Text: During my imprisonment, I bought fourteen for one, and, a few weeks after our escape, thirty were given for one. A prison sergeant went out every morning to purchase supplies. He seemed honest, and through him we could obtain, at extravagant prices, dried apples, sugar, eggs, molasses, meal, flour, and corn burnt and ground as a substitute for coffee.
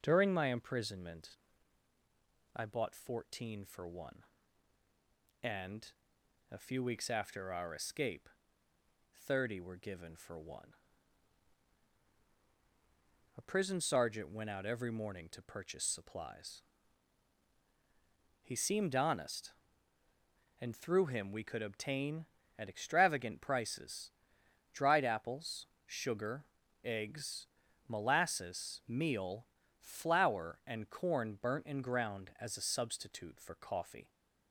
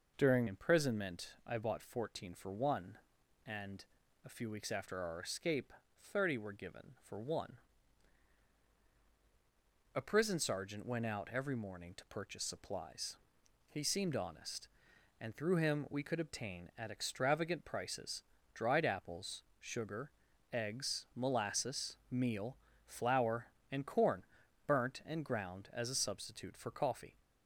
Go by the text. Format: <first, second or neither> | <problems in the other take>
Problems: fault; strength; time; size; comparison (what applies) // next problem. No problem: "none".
first | skips "my"; at 0.4 s // pauses between "corn" and "burnt"; at 24.2 s; 0.40 s long